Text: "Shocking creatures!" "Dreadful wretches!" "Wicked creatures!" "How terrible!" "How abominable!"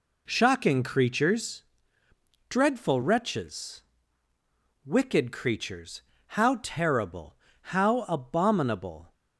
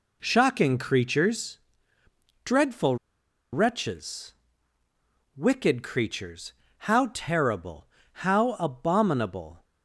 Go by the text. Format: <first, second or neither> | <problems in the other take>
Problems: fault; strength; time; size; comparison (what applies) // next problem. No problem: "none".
first | pauses between "Dreadful" and "wretches"; noticeable; at 2.9 s; 0.57 s long